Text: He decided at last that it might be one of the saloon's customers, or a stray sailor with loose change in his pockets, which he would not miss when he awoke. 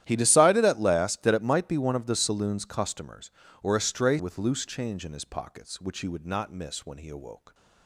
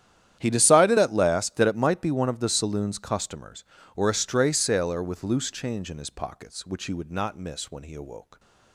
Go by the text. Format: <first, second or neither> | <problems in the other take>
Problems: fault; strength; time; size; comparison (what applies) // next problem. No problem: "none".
second | starts louder than the rest; strong; until 1.0 s; 12 dB; strong in the second // skips "sailor"; at 4.1 s